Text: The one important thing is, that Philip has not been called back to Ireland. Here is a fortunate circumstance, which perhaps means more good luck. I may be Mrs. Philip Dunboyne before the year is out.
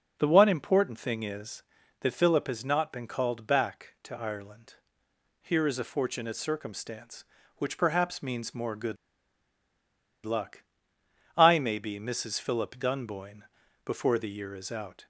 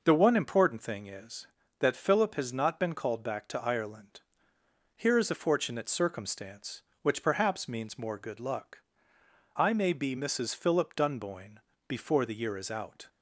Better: second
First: pauses between "good" and "luck"; strong; at 8.9 s; 1.2 s long // pauses between "Dunboyne" and "before"; at 13.4 s; 0.42 s long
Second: pauses between "Dunboyne" and "before"; slight; at 11.5 s; 0.30 s long

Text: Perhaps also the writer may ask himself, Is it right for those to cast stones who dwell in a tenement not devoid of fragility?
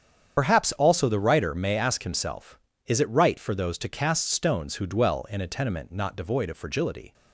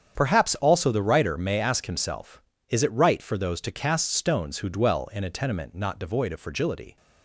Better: second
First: loses the start of "Perhaps"; at 0.3 s; 50 ms // starts louder than the rest; strong; until 1.4 s; 8 dB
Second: starts louder than the rest; strong; until 1.1 s; 8 dB

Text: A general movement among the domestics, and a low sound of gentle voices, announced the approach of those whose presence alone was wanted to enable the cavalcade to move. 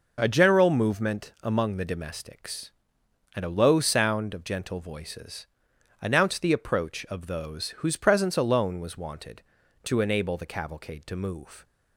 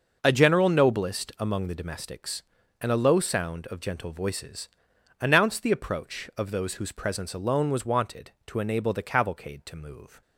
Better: first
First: none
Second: says "noblest" for "movement"; at 0.6 s

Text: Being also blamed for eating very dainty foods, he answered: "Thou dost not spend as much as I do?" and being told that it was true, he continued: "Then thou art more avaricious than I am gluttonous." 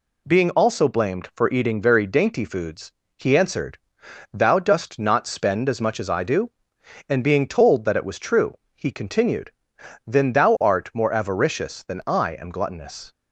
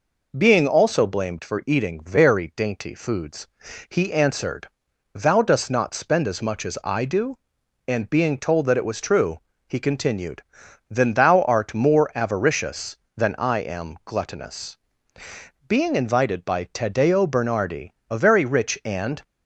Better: first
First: none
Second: goes on to say "Being invited by Taddeo Bernardi a very rich and"; strong; from 15.6 s on; 3.5 s long

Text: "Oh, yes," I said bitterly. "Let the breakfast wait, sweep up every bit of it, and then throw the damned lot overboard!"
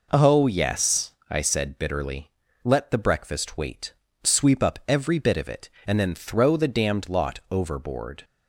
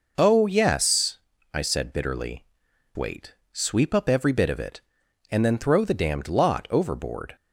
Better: first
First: none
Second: skips "Let the breakfast"; at 2.6 s

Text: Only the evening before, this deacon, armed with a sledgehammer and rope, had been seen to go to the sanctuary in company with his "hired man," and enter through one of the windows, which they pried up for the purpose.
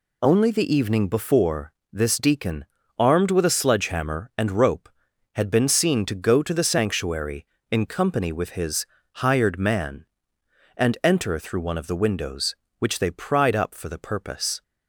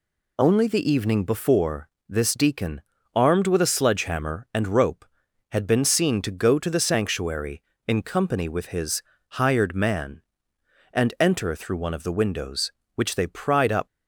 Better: first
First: pauses between "his" and "hired"; slight; at 8.8 s; 0.30 s long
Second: pauses between "his" and "hired"; slight; at 9.0 s; 0.30 s long // stops before "for the purpose"; at 13.8 s

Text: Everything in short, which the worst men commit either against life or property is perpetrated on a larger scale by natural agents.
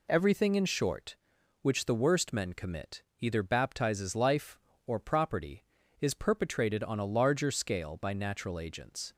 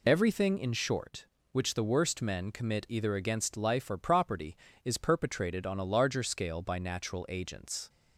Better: second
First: pauses between "commit" and "either"; slight; at 3.0 s; 0.16 s long // says "baptizes" for "against"; at 3.4 s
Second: none

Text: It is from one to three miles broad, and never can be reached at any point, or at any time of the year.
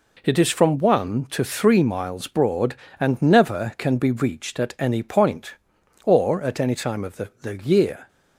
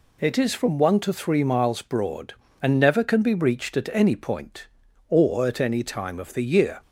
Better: second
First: says "the" twice; at 7.4 s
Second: none

